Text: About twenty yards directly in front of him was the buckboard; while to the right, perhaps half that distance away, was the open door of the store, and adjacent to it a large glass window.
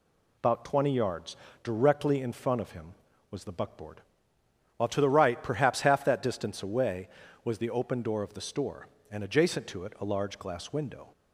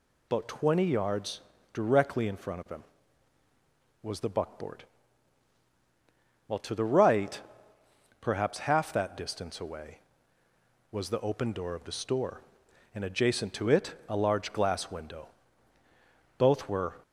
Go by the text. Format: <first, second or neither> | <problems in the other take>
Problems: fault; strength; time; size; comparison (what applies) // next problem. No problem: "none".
first | pauses between "yards" and "directly"; slight; at 1.4 s; 0.32 s long; slight in the first // goes on to say "Both were"; from 16.3 s on; 0.58 s long